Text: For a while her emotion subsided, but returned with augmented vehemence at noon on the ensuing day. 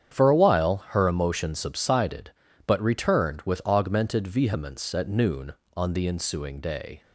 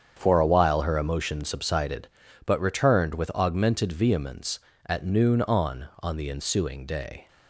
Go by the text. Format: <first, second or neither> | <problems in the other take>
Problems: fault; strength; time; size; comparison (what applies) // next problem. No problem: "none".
first | starts louder than the rest; strong; until 1.1 s; 7.5 dB; strong in the first // says "on" twice; at 6.0 s